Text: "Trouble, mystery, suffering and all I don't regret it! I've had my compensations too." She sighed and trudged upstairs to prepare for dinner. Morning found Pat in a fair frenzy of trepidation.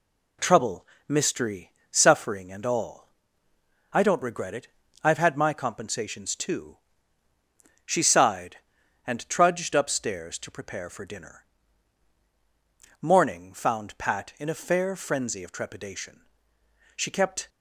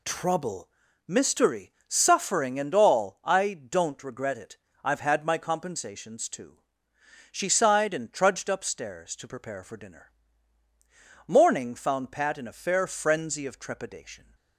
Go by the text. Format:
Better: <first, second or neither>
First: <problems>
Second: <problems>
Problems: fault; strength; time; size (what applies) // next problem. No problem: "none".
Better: second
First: pauses between "all" and "I"; noticeable; at 3.0 s; 0.82 s long // goes on to say "She kept"; from 16.9 s on; 0.54 s long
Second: none